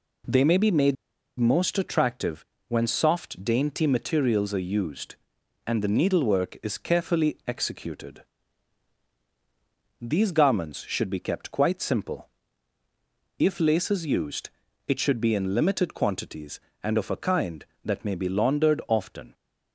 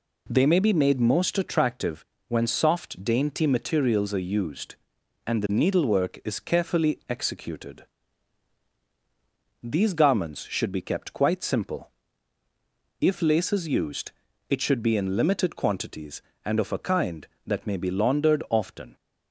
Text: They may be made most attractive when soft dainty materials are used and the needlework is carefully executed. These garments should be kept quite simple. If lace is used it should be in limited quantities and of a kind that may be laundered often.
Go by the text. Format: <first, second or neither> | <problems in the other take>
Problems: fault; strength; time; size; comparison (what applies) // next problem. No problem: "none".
second | pauses between "made" and "most"; at 0.9 s; 0.44 s long // pauses between "attractive" and "when"; slight; at 2.4 s; 0.24 s long; slight in the second // pauses between "used" and "it"; at 14.4 s; 0.38 s long; also in the second